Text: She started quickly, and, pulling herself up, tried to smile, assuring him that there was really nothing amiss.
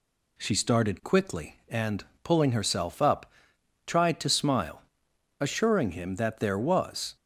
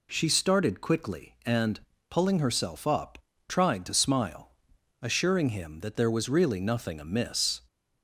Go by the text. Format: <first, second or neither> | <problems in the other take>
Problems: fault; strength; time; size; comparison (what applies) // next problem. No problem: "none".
second | stops before "really nothing amiss"; at 7.1 s